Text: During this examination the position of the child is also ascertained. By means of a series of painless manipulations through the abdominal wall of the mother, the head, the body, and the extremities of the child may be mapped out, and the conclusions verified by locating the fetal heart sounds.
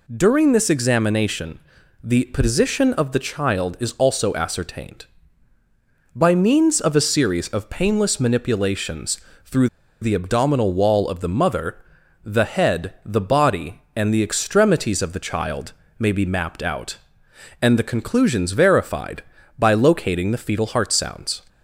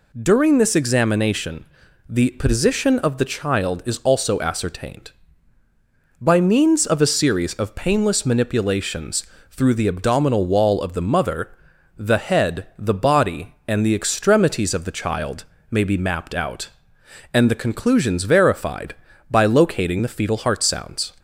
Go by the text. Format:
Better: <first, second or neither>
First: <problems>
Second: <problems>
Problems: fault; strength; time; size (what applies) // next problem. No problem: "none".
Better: second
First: pauses between "examination" and "the"; at 1.5 s; 0.42 s long // pauses between "manipulations" and "through"; slight; at 9.1 s; 0.26 s long // pauses between "through" and "the"; slight; at 9.6 s; 0.35 s long // pauses between "child" and "may"; slight; at 15.7 s; 0.24 s long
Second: pauses between "examination" and "the"; at 1.6 s; 0.42 s long // pauses between "manipulations" and "through"; slight; at 9.2 s; 0.26 s long // pauses between "child" and "may"; slight; at 15.4 s; 0.24 s long